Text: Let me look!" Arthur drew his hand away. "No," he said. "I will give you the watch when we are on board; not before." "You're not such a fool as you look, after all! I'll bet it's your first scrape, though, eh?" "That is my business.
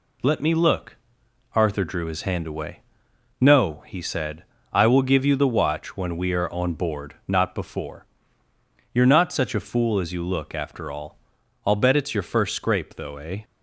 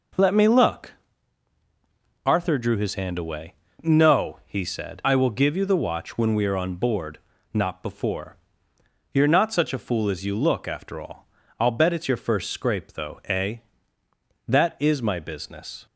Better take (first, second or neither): second